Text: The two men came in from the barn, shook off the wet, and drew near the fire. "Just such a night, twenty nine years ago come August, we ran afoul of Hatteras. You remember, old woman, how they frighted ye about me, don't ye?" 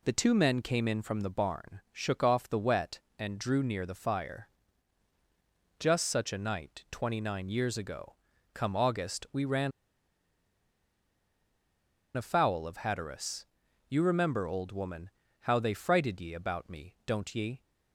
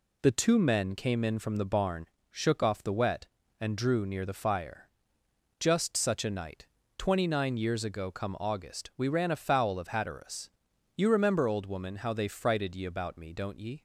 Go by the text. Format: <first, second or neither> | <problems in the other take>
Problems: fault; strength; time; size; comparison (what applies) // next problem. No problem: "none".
second | pauses between "ago" and "come"; slight; at 8.1 s; 0.36 s long // pauses between "ran" and "afoul"; strong; at 9.7 s; 2.4 s long